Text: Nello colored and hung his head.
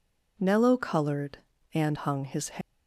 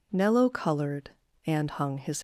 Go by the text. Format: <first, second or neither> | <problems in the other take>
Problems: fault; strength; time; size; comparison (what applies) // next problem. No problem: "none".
first | stops before "head"; at 2.1 s